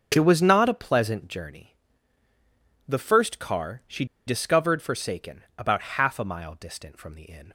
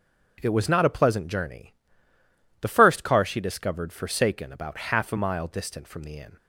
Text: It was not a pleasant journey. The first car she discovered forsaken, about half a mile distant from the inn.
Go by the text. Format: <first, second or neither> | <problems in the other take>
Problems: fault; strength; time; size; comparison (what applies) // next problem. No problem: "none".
second | starts louder than the rest; until 1.1 s; 6.5 dB; also in the second // pauses between "she" and "discovered"; slight; at 4.0 s; 0.22 s long